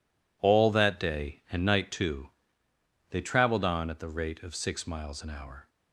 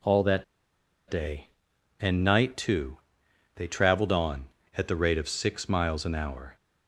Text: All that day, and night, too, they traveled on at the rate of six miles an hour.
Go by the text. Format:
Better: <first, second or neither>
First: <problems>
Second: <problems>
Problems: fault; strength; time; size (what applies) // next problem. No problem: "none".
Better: first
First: none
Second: pauses between "that" and "day"; noticeable; at 0.4 s; 0.65 s long